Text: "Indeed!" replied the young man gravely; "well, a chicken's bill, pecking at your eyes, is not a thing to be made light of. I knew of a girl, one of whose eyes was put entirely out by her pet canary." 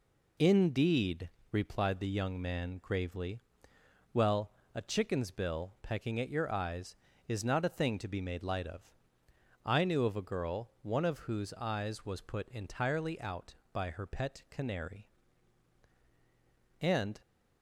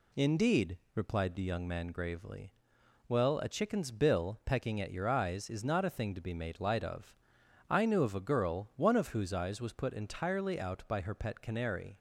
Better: second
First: goes on to say "And"; slight; from 16.8 s on; 0.38 s long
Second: none

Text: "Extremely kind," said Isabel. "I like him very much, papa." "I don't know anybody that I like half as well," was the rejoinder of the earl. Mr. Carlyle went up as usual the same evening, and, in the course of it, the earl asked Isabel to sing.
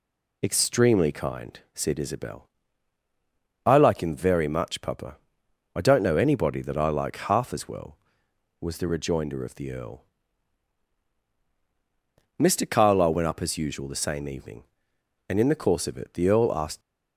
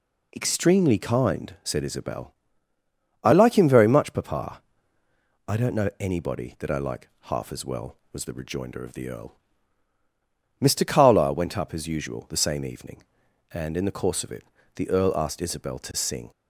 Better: second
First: stops before "Isabel to sing"; at 16.8 s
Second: none

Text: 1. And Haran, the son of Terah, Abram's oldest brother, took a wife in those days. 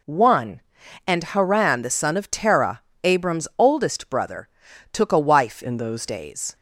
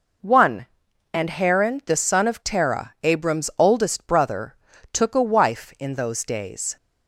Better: second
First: changes voice from "in" to "those"; from 5.6 to 6.0 s; 0.4 s long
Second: none

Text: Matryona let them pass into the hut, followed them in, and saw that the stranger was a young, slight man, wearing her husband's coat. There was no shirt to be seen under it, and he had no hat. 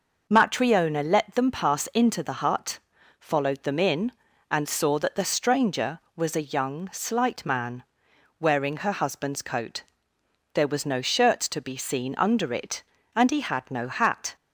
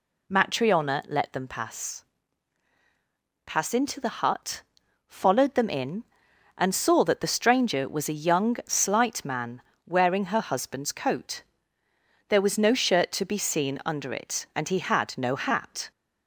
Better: first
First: none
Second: says "pass" twice; at 3.4 s

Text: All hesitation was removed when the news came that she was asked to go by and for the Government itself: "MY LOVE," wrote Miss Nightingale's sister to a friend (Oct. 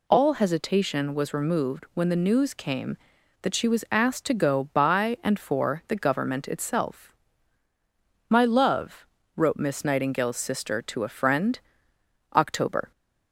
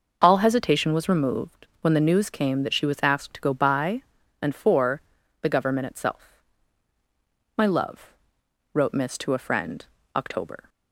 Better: first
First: none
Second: pauses between "for" and "the"; at 5.0 s; 0.40 s long // skips "Nightingale's sister"; at 9.1 s

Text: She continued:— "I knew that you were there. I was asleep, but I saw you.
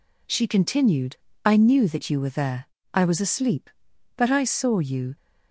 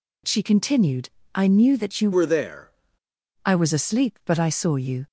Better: first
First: none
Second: changes voice from "were" to "there"; from 2.1 to 2.7 s; 0.6 s long

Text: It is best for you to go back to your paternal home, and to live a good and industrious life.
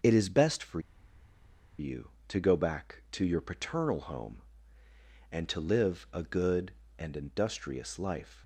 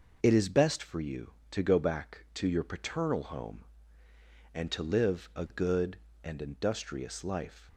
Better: second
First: pauses between "for" and "you"; at 0.7 s; 0.99 s long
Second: none

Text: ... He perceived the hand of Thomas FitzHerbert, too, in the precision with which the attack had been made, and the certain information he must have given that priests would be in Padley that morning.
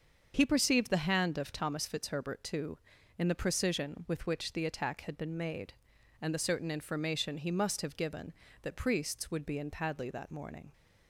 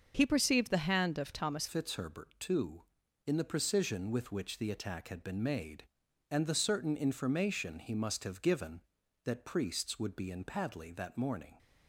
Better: first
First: starts louder than the rest; until 1.3 s; 7 dB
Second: starts louder than the rest; until 1.1 s; 6.5 dB // changes voice at "FitzHerbert"; from 1.6 s on; 9.9 s long

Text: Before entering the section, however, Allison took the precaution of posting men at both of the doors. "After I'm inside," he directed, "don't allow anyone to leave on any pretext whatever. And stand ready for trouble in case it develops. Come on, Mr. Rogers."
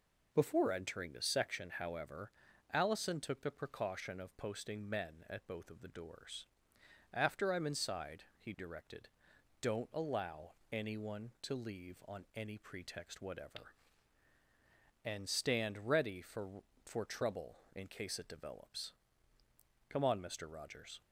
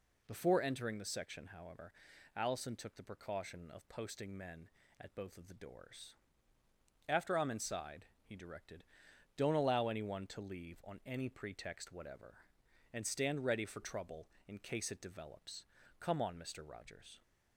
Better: second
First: pauses between "allow" and "anyone"; slight; at 10.5 s; 0.18 s long // says "for" twice; at 16.8 s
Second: none

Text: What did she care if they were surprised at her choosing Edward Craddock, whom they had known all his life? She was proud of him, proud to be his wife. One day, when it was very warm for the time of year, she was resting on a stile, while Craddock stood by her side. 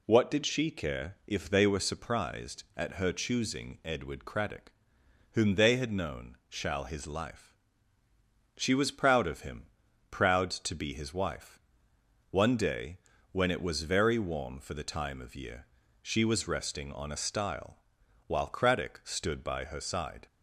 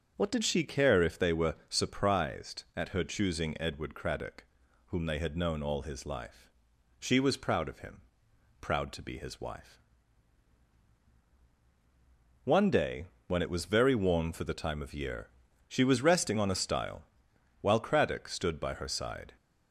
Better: second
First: says "shall" for "all"; at 6.4 s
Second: none

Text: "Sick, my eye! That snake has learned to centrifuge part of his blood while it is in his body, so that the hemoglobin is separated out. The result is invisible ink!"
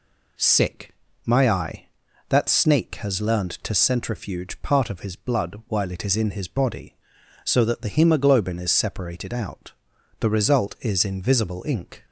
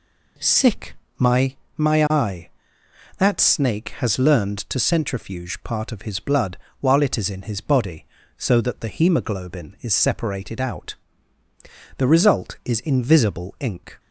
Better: first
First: none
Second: says "my" twice; at 1.7 s // pauses between "blood" and "while"; slight; at 6.5 s; 0.24 s long

